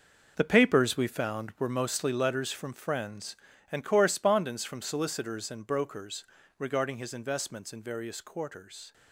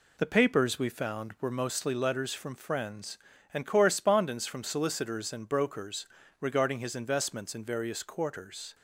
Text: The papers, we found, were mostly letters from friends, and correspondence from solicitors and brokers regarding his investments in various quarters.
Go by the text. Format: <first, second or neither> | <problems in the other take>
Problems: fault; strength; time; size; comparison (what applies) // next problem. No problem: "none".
second | gets quieter; strong; throughout; 11.5 dB // pauses between "brokers" and "regarding"; slight; at 6.2 s; 0.32 s long; slight in the second